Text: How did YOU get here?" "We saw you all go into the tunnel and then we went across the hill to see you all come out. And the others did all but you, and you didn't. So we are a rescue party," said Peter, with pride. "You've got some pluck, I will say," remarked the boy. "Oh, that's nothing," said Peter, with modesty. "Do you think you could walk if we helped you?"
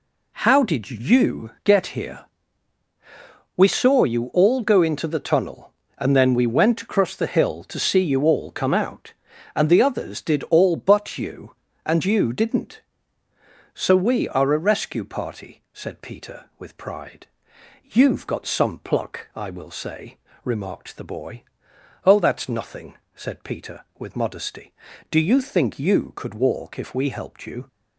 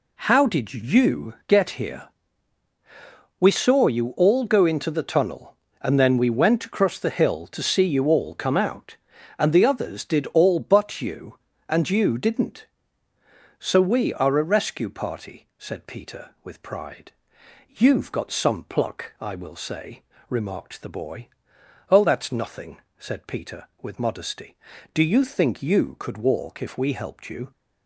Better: neither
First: none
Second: none

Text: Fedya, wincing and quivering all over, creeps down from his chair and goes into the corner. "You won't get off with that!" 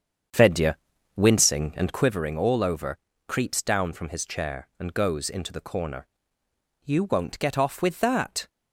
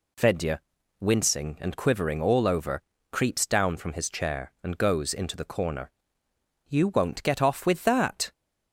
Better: second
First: starts louder than the rest; strong; until 2.2 s; 7.5 dB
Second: none

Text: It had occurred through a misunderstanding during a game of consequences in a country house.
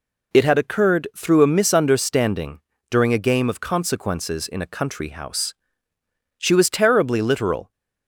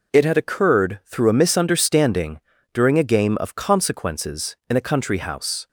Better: second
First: pauses between "misunderstanding" and "during"; slight; at 2.6 s; 0.28 s long // goes on to say "She was terribly literal"; from 6.3 s on; 1.3 s long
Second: pauses between "misunderstanding" and "during"; slight; at 2.3 s; 0.34 s long

